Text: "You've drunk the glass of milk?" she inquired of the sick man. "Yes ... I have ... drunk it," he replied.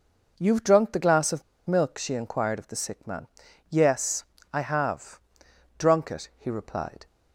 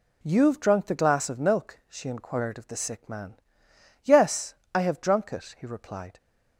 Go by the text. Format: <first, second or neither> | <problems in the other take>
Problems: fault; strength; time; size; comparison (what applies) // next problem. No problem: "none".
second | pauses between "of" and "milk"; slight; at 1.4 s; 0.26 s long